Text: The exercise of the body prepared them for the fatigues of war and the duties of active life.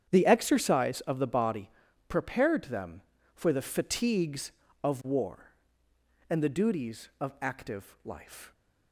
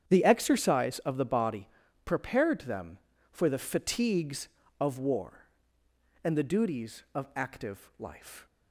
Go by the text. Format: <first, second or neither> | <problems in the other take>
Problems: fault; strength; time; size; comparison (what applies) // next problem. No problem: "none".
neither | starts louder than the rest; strong; the same in both // pauses between "body" and "prepared"; the same in both